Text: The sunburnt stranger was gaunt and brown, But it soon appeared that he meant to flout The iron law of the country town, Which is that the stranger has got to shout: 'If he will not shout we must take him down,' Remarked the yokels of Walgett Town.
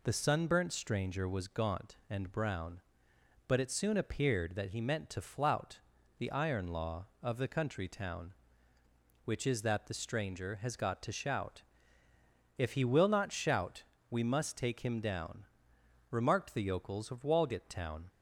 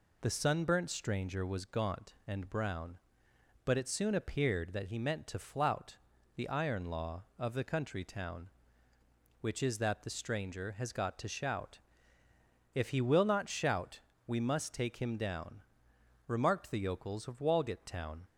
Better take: neither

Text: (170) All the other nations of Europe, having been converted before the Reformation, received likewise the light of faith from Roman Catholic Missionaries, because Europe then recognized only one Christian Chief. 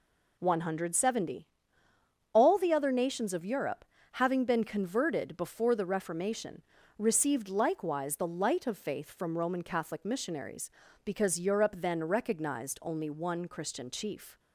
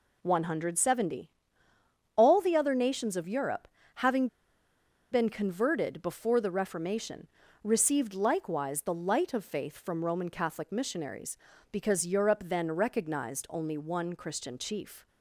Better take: first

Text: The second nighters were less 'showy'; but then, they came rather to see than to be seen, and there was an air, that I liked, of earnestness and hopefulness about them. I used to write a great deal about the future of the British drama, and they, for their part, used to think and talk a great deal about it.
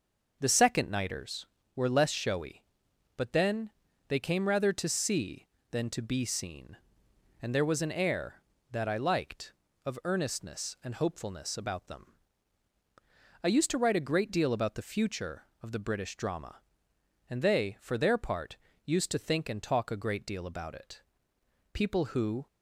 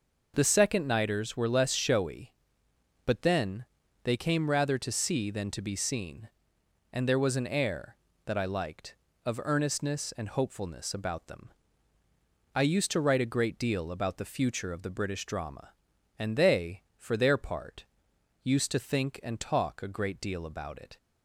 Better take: second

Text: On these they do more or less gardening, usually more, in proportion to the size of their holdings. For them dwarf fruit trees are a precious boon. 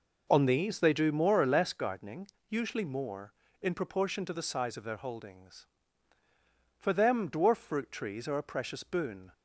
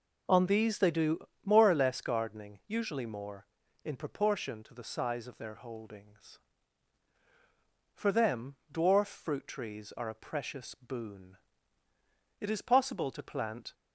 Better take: first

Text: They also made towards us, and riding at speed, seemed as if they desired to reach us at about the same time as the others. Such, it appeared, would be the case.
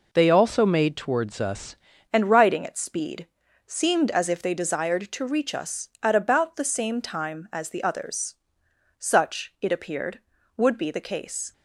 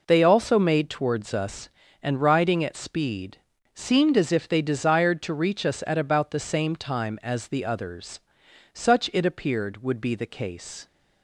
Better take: second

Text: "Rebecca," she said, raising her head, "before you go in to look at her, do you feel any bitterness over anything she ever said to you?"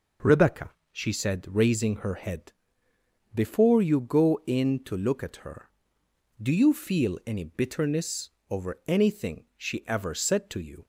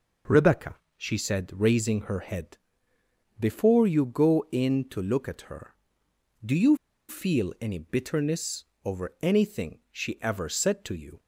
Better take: first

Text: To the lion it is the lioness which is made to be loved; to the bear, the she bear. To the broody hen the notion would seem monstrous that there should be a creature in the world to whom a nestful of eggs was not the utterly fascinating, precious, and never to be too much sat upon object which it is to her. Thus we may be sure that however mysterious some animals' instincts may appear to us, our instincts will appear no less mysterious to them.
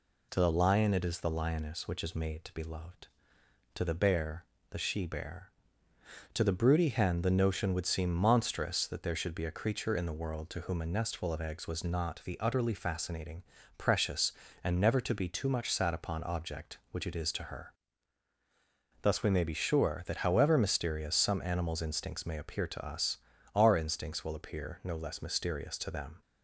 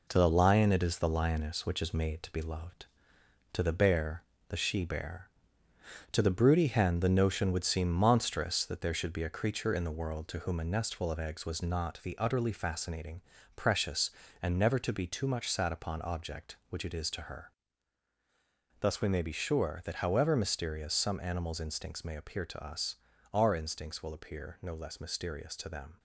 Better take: first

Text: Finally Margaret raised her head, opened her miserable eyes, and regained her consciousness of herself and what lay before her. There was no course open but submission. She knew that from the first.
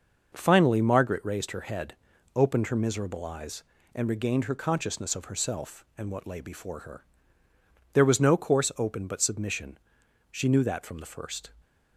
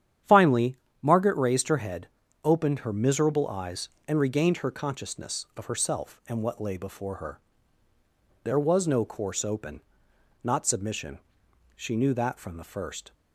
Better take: first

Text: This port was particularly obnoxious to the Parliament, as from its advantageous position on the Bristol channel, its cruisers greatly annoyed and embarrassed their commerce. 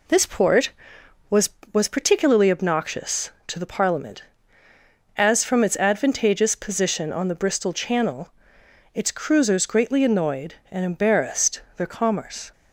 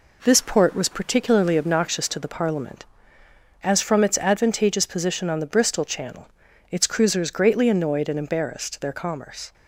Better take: second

